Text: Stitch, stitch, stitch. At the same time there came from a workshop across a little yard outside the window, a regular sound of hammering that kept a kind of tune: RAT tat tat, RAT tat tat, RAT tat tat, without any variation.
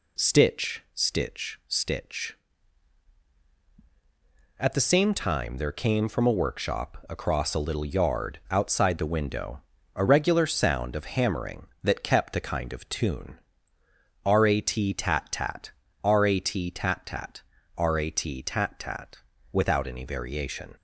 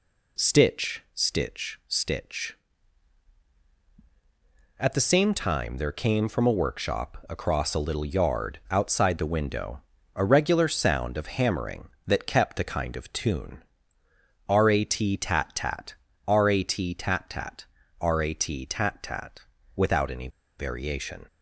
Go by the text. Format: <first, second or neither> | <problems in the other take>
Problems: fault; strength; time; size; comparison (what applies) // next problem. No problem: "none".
first | pauses between "any" and "variation"; slight; at 20.2 s; 0.30 s long